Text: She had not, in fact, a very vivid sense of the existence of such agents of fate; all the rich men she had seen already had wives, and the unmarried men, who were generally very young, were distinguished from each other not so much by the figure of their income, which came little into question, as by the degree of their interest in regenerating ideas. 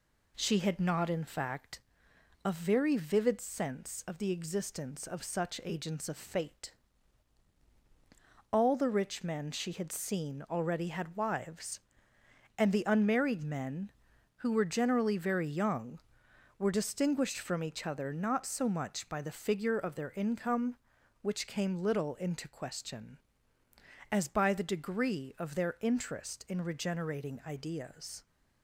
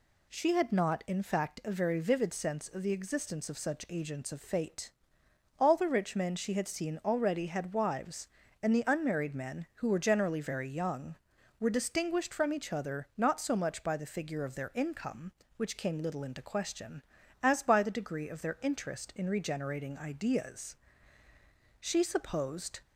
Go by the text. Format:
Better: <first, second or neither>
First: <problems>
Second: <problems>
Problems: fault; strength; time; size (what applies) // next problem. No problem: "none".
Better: first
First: none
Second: goes on to say "She supposed"; noticeable; from 21.7 s on; 1.0 s long